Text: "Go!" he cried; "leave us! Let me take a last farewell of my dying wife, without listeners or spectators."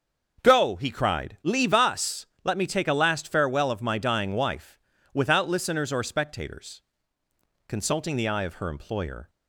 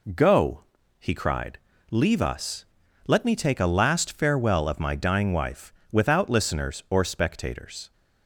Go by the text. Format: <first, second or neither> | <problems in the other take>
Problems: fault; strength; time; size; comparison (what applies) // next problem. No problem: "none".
second | starts louder than the rest; until 1.4 s; 6.5 dB // goes on to say "Consulting the eye of her employer"; from 7.6 s on; 1.6 s long